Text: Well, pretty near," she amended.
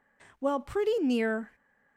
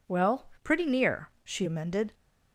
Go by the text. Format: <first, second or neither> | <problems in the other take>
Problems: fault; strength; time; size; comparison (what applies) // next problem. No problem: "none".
second | stops before "she amended"; at 1.5 s